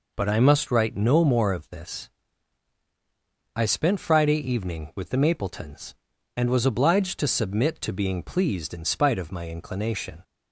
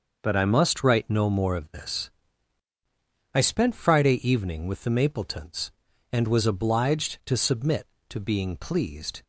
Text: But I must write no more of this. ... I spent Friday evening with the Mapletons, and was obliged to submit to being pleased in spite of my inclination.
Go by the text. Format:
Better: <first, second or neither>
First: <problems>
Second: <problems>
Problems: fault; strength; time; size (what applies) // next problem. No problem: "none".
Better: first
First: none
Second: starts louder than the rest; noticeable; until 1.2 s; 6 dB // stops before "in spite of my inclination"; at 9.2 s